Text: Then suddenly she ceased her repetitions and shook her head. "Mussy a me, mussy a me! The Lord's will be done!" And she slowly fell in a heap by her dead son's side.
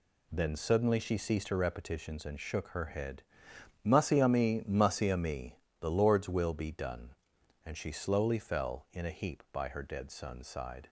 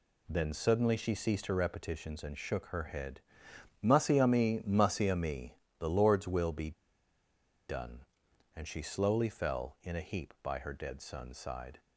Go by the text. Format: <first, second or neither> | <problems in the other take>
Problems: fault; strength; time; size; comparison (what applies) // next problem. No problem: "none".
first | pauses between "be" and "done"; noticeable; at 6.7 s; 0.94 s long